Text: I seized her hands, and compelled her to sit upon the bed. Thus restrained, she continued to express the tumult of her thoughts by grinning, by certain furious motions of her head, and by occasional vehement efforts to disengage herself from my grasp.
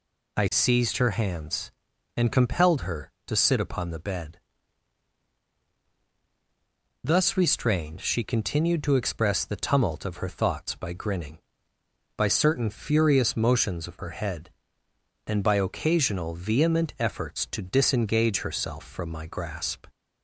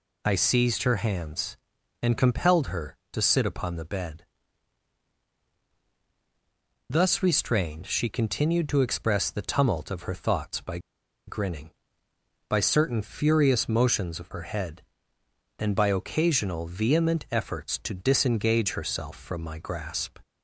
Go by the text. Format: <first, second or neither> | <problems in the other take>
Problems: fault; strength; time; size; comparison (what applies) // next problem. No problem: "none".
first | pauses between "by" and "grinning"; noticeable; at 10.7 s; 0.48 s long